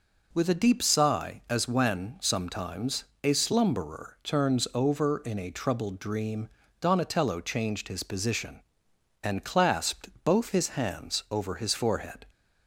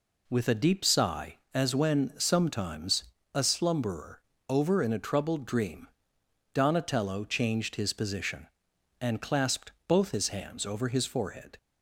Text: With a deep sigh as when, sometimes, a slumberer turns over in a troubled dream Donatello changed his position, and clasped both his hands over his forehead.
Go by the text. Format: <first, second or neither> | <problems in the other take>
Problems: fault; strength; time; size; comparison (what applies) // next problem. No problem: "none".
first | skips "turns"; at 4.3 s // pauses between "dream" and "Donatello"; noticeable; at 5.8 s; 0.66 s long; slight in the first // pauses between "clasped" and "both"; slight; at 9.7 s; 0.16 s long; slight in the first